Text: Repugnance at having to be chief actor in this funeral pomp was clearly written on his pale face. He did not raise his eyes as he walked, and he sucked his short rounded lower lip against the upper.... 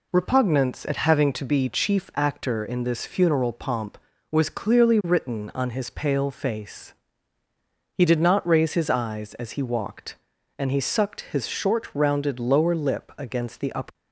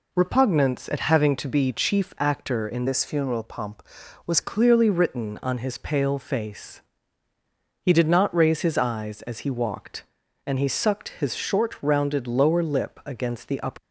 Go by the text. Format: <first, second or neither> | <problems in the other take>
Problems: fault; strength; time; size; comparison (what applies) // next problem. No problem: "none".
first | changes voice from "this" to "was"; from 2.8 to 4.3 s; 1.5 s long